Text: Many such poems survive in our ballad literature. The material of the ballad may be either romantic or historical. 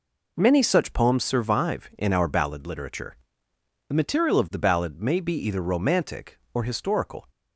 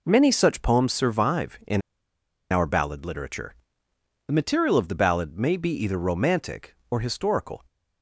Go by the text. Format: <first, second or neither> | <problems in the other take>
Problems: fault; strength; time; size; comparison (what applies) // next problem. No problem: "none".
first | pauses between "in" and "our"; noticeable; at 1.8 s; 0.70 s long